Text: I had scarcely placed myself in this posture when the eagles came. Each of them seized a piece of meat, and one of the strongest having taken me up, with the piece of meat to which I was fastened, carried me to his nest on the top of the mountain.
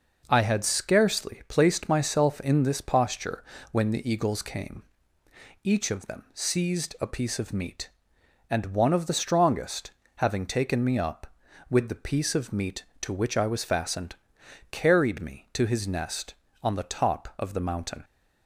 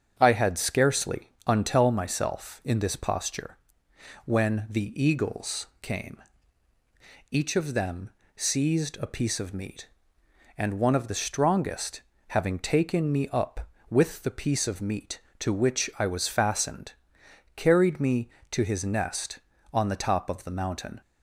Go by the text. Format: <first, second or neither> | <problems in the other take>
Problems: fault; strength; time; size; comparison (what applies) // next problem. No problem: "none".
first | starts louder than the rest; strong; until 1.1 s; 7.5 dB // says "untell" for "placed"; at 1.4 s // pauses between "posture" and "when"; noticeable; at 3.5 s; 0.66 s long; slight in the first // pauses between "eagles" and "came"; slight; at 5.6 s; 0.16 s long // pauses between "them" and "seized"; slight; at 8.0 s; 0.26 s long // pauses between "strongest" and "having"; slight; at 12.0 s; 0.28 s long; slight in the first